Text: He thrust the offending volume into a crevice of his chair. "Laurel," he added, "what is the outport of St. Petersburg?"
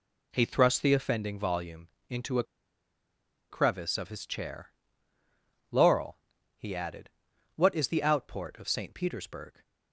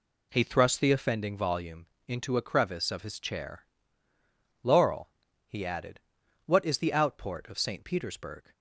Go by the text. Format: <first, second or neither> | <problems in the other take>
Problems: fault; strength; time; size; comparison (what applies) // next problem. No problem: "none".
second | pauses between "volume" and "into"; slight; at 1.8 s; 0.18 s long; slight in the second // pauses between "a" and "crevice"; at 2.4 s; 1.0 s long